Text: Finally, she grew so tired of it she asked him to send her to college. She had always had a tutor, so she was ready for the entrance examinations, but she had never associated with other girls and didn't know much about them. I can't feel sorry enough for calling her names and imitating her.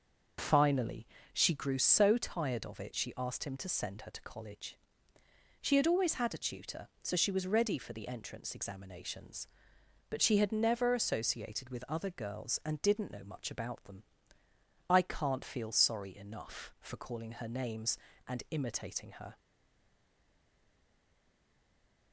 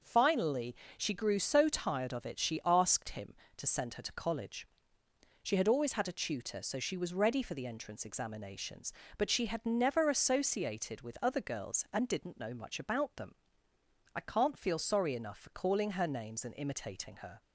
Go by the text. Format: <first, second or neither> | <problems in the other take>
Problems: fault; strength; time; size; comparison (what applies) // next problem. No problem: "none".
second | stays silent after the last word; strong; from 19.3 s on; 2.8 s long